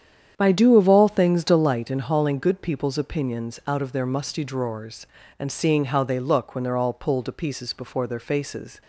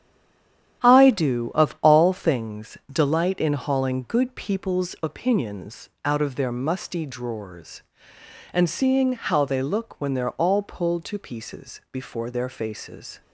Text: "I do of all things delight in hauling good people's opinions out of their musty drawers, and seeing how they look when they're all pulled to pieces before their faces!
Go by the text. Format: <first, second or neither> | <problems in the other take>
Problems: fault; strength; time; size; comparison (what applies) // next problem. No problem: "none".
first | stays silent before the first word; slight; until 0.8 s; 0.8 s long // starts louder than the rest; strong; until 1.9 s; 10.5 dB; strong in the first // pauses between "things" and "delight"; slight; at 2.7 s; 0.16 s long // pauses between "opinions" and "out"; slight; at 5.8 s; 0.16 s long